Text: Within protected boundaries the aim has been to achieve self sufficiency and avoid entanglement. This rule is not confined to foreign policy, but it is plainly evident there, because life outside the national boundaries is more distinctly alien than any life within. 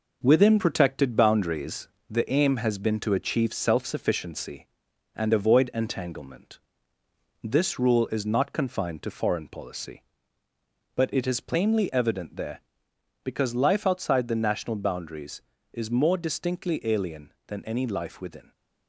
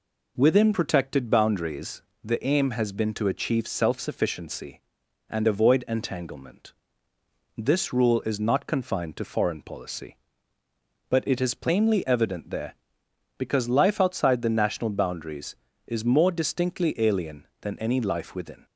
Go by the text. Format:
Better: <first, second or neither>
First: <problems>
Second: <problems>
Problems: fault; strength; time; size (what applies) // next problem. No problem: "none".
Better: second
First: gets quieter; noticeable; throughout; 5 dB // pauses between "boundaries" and "the"; slight; at 1.8 s; 0.20 s long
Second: pauses between "boundaries" and "the"; slight; at 2.0 s; 0.20 s long